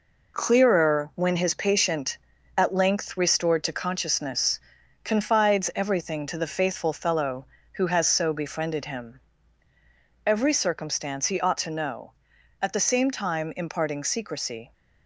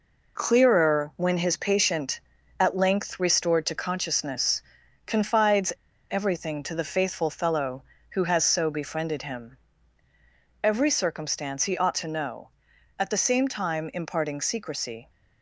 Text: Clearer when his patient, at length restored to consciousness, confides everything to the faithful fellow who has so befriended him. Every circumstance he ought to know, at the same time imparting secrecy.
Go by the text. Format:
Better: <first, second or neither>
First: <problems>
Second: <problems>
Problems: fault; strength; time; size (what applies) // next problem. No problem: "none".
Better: first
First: none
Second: pauses between "confides" and "everything"; at 5.7 s; 0.39 s long